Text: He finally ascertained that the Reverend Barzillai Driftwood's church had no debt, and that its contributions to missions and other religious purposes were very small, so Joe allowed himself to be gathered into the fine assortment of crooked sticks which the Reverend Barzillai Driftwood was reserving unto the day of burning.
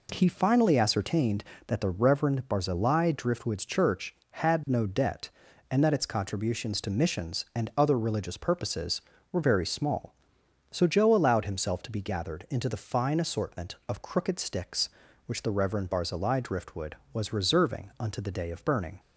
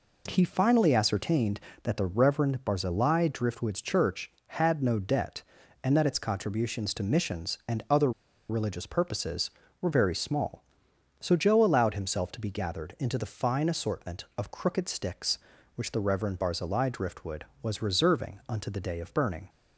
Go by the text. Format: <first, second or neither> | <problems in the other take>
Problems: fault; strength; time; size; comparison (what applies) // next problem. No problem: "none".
first | pauses between "other" and "religious"; at 8.1 s; 0.39 s long